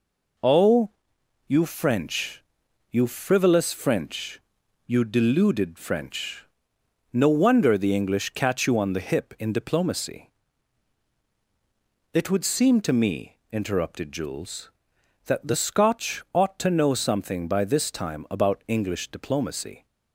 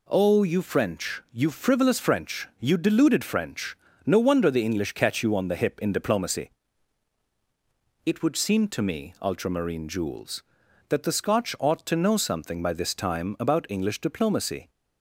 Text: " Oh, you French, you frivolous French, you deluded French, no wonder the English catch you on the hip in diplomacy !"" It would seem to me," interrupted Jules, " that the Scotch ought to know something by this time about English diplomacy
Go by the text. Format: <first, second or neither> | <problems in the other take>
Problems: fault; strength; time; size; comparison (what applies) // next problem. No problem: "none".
first | says "ultramarine" for "interrupted"; at 9.2 s